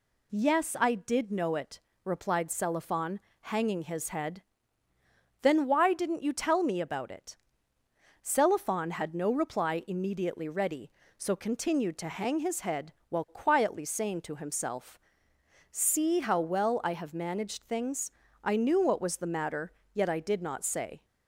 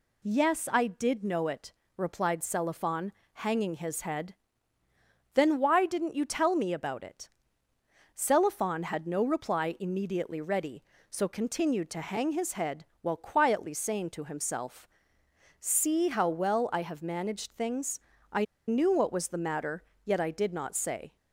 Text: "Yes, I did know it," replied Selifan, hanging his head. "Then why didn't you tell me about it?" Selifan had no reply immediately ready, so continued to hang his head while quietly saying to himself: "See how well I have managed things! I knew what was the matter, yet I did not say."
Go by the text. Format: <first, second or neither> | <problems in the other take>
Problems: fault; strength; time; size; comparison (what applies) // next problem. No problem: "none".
first | pauses between "head" and "while"; slight; at 12.8 s; 0.16 s long; slight in the first // pauses between "I" and "knew"; slight; at 18.4 s; 0.22 s long